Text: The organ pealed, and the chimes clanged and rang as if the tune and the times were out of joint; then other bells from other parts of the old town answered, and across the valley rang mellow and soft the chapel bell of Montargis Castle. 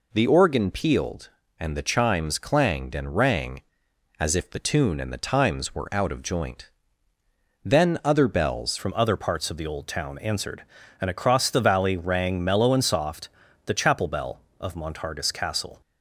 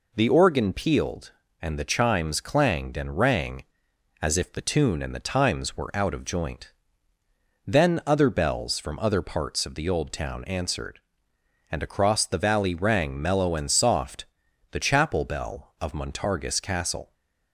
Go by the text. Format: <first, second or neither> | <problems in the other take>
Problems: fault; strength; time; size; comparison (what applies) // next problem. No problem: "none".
second | changes voice at "from"; from 8.7 s on; 7.1 s long // pauses between "soft" and "the"; slight; at 13.3 s; 0.34 s long; also in the second